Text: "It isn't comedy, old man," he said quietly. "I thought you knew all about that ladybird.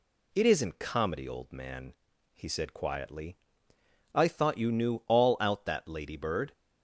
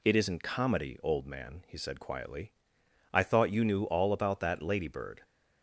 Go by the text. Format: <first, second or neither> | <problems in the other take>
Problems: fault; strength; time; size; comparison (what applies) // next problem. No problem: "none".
second | says "out" for "about"; at 5.4 s